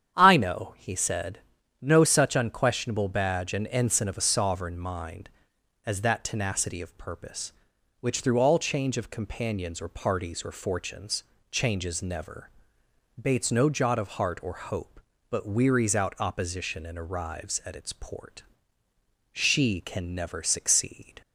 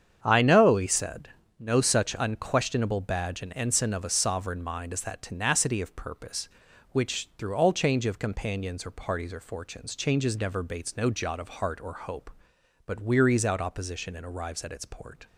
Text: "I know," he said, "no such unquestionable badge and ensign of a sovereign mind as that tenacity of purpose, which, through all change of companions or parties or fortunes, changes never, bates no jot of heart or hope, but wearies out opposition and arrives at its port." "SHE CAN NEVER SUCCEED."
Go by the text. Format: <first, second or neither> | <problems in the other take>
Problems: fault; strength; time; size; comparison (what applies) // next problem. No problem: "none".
first | starts louder than the rest; strong; until 1.2 s; 8 dB; strong in the first // stops before "SHE CAN NEVER SUCCEED"; at 15.2 s